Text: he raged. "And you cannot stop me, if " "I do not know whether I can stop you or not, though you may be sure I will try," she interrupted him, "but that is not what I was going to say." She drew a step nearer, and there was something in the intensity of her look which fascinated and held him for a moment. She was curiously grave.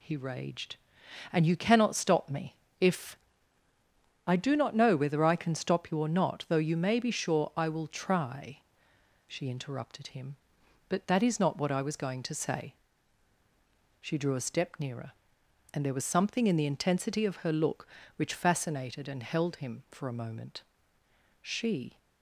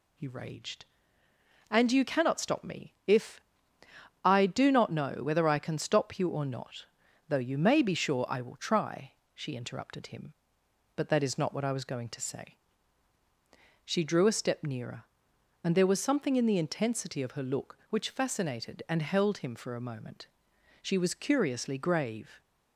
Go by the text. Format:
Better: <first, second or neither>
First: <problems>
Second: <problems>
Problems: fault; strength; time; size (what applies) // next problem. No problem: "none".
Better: second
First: stops before "was curiously grave"; at 21.9 s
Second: none